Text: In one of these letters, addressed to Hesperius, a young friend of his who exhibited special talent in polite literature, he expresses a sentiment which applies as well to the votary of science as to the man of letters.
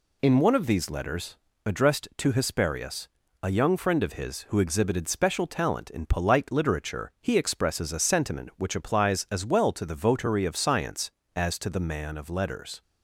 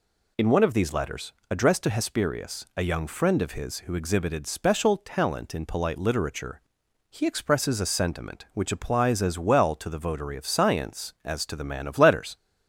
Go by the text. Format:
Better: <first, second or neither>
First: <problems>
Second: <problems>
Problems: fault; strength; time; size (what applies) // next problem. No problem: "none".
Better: neither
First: none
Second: none